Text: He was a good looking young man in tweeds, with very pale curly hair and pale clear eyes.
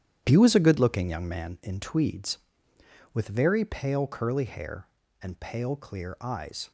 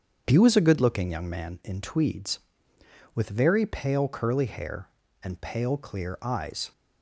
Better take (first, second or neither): second